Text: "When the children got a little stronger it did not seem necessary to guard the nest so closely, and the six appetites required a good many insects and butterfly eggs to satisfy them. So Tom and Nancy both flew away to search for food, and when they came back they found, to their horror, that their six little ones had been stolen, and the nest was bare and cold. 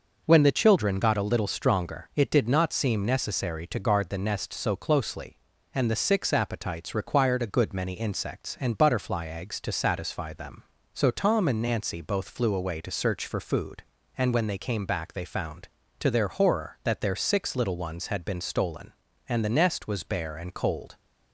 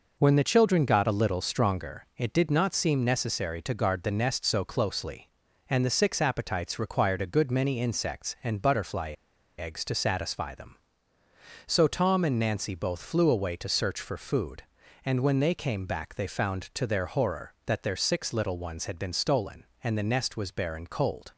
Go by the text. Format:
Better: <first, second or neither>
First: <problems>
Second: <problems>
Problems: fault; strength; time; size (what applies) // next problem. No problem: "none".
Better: first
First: none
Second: pauses between "butterfly" and "eggs"; at 9.1 s; 0.45 s long